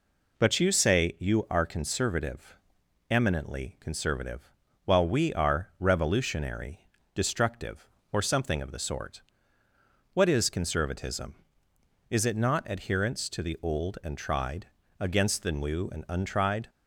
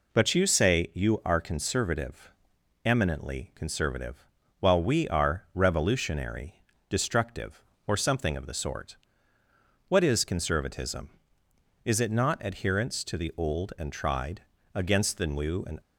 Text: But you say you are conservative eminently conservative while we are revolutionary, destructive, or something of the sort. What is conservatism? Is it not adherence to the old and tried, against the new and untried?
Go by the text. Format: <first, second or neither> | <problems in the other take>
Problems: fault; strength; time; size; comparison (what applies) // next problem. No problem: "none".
first | pauses between "conservative" and "eminently"; noticeable; at 2.3 s; 0.54 s long; noticeable in the first // pauses between "conservative" and "while"; slight; at 4.2 s; 0.34 s long; slight in the first // stops before "untried"; at 15.8 s